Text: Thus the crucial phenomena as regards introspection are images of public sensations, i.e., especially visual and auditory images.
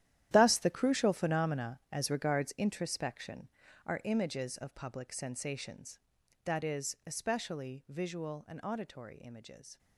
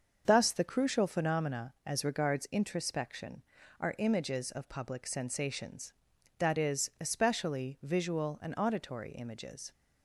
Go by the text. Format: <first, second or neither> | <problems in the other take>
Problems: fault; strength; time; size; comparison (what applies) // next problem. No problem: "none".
second | gets quieter; strong; throughout; 14 dB // starts louder than the rest; strong; until 1.3 s; 12 dB; also in the second